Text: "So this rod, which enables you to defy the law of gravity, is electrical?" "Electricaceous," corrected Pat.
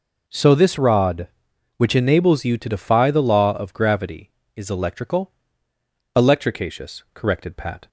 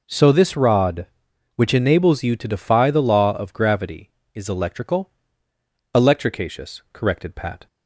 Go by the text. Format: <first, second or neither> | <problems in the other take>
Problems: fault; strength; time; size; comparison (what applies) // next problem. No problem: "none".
neither | none